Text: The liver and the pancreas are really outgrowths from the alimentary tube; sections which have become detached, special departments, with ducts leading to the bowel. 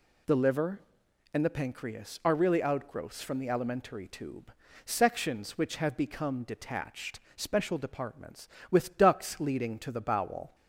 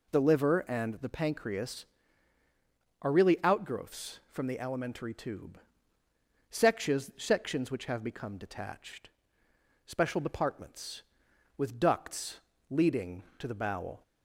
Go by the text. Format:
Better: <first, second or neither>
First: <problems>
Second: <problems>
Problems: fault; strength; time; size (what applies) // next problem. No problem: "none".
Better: first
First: none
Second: says "sections" twice; at 7.1 s // pauses between "ducts" and "leading"; slight; at 12.4 s; 0.30 s long